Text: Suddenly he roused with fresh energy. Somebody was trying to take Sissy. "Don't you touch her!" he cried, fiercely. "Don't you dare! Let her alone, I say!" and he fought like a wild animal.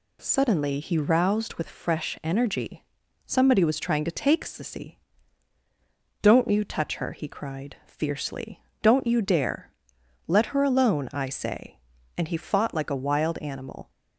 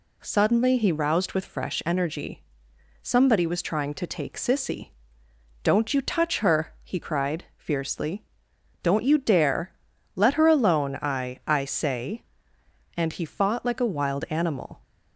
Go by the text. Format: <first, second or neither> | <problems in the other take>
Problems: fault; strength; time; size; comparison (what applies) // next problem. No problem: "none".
first | says "I" twice; at 11.4 s